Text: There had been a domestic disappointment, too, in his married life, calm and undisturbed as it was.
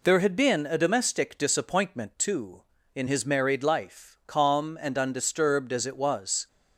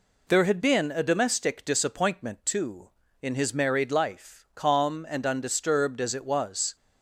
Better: neither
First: none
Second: none

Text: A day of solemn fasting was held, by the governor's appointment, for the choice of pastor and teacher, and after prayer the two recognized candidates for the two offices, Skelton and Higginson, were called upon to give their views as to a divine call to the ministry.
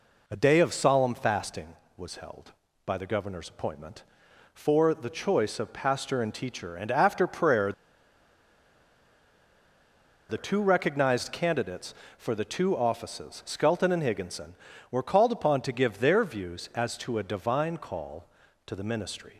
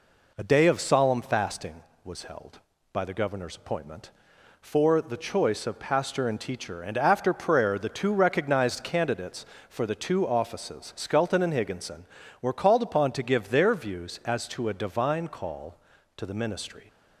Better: second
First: pauses between "prayer" and "the"; strong; at 7.7 s; 2.5 s long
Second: none

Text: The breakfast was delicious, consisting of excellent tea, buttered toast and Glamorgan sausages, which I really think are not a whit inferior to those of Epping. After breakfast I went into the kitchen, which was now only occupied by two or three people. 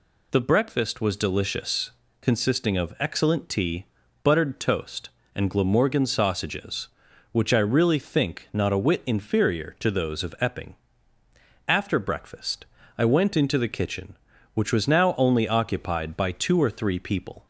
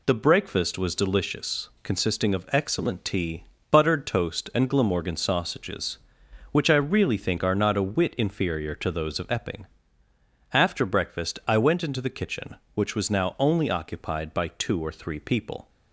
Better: second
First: skips "are"; at 8.4 s // pauses between "breakfast" and "I"; slight; at 12.6 s; 0.32 s long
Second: none

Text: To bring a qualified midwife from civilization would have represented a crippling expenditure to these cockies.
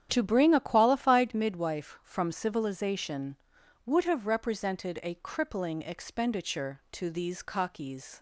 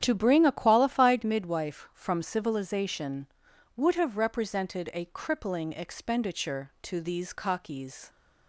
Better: neither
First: starts louder than the rest; strong; until 1.1 s; 9.5 dB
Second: starts louder than the rest; strong; until 1.0 s; 9.5 dB

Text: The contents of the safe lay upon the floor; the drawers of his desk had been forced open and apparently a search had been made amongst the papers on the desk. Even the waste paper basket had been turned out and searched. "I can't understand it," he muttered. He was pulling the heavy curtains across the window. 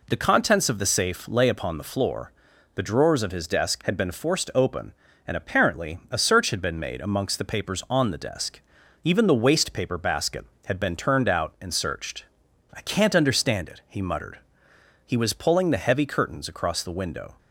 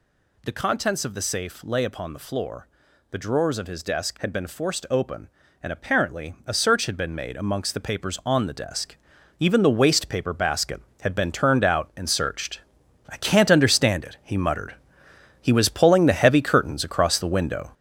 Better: first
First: none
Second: gets louder; throughout; 6.5 dB

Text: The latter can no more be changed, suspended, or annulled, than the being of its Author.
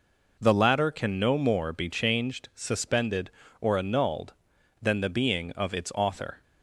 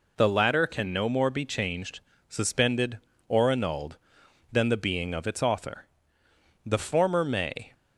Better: first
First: none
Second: goes on to say "The former may"; noticeable; from 6.6 s on; 1.1 s long

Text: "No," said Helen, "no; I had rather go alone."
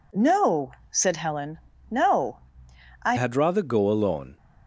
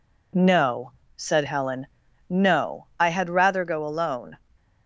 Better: second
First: changes voice at "had"; from 3.1 s on; 1.2 s long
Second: none

